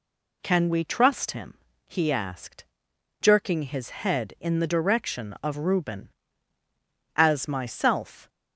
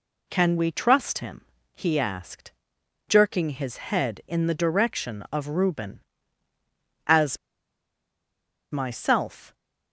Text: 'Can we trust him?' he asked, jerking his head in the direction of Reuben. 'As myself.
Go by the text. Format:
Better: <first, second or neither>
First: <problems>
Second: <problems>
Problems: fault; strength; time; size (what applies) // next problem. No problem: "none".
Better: first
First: none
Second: pauses between "As" and "myself"; strong; at 7.3 s; 1.3 s long